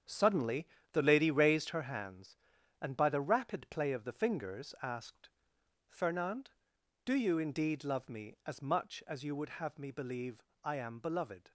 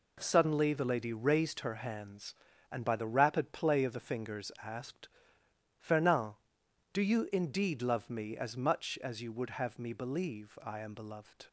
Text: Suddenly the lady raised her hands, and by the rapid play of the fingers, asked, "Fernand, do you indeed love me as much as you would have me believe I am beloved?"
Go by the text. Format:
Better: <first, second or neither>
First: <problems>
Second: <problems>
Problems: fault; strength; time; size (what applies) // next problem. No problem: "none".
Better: second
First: gets quieter; strong; throughout; 9.5 dB // pauses between "Suddenly" and "the"; slight; at 0.6 s; 0.26 s long // pauses between "believe" and "I"; slight; at 10.4 s; 0.22 s long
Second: none